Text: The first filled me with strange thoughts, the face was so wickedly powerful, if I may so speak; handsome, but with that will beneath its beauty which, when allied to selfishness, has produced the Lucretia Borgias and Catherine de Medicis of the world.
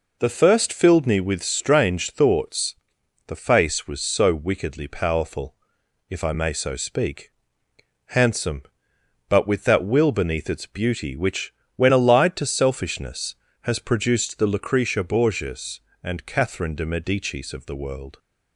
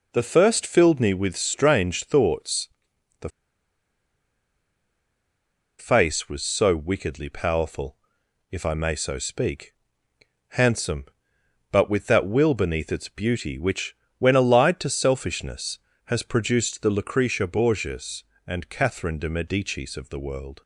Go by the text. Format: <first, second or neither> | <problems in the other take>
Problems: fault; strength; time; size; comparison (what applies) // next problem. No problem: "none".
first | pauses between "the" and "face"; strong; at 3.2 s; 2.5 s long